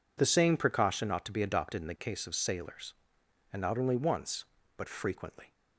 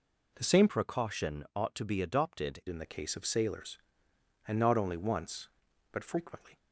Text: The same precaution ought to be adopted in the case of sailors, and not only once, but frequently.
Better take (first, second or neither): first